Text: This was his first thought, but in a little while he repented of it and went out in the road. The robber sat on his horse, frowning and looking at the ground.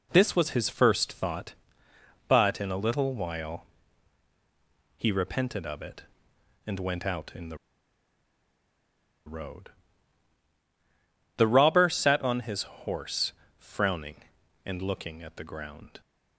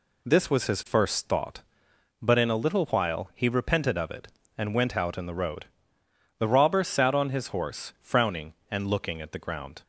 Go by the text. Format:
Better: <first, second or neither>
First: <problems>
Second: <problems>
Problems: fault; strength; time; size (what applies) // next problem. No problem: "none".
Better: second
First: pauses between "while" and "he"; strong; at 3.6 s; 1.3 s long // pauses between "the" and "road"; strong; at 7.5 s; 1.6 s long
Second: none